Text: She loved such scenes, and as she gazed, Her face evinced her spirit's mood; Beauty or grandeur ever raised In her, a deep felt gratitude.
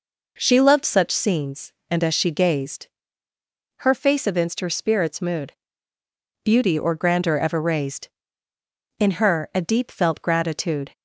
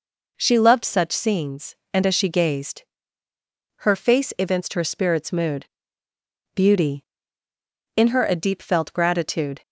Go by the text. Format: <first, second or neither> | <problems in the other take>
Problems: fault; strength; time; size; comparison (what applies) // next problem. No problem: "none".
first | skips "or grandeur ever raised"; at 7.5 s